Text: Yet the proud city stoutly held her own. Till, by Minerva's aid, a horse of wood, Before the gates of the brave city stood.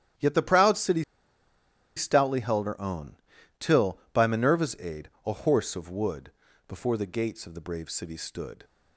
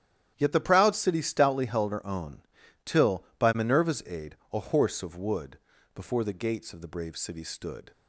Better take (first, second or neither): second